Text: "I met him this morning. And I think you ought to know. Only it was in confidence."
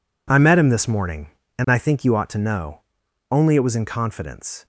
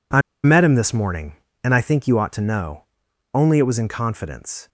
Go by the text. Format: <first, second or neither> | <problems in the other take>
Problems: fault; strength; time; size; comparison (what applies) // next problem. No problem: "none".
first | pauses between "I" and "met"; slight; at 0.1 s; 0.24 s long